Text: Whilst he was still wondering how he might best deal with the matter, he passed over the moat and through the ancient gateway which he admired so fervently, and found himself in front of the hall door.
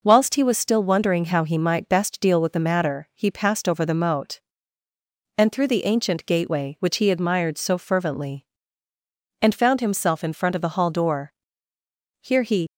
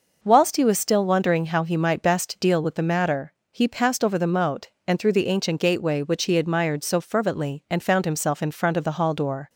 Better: second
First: goes on to say "Here he"; slight; from 12.2 s on; 0.46 s long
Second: none

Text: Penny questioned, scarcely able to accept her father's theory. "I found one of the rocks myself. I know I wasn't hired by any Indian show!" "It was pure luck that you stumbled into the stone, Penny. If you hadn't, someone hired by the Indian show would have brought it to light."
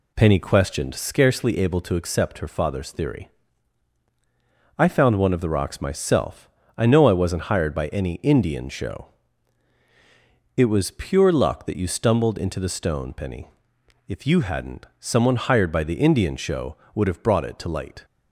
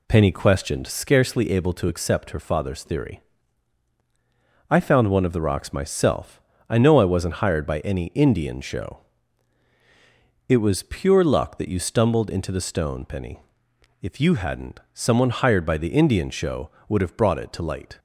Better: neither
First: none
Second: none

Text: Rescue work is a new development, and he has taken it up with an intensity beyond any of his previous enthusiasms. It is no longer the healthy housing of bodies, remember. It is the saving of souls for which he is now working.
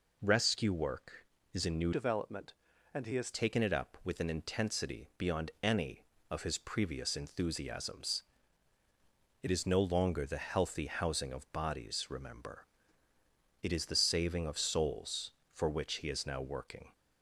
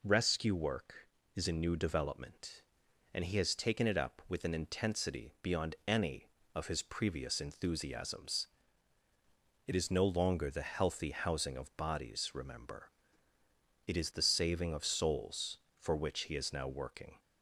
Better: second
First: changes voice from "development" to "has"; from 1.9 to 3.3 s; 1.4 s long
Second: none

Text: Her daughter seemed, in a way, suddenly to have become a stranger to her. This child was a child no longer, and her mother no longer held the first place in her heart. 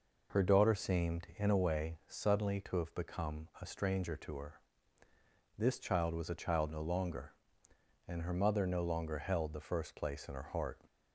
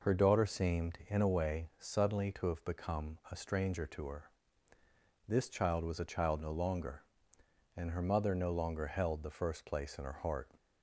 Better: neither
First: none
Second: none

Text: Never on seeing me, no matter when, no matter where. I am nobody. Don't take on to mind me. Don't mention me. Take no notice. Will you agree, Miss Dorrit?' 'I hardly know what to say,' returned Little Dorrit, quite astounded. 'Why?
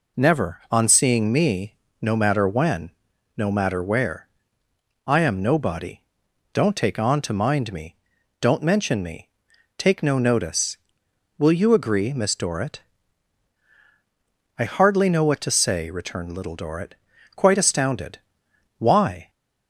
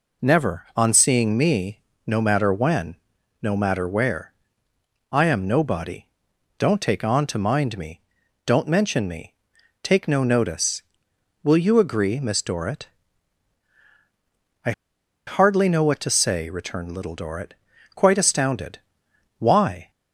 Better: first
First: none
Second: pauses between "I" and "hardly"; noticeable; at 14.7 s; 0.55 s long

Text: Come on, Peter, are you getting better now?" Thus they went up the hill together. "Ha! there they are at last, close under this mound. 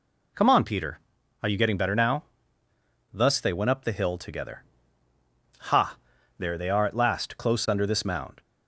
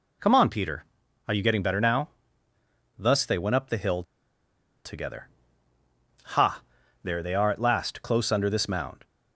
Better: first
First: none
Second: pauses between "hill" and "together"; noticeable; at 4.0 s; 0.81 s long

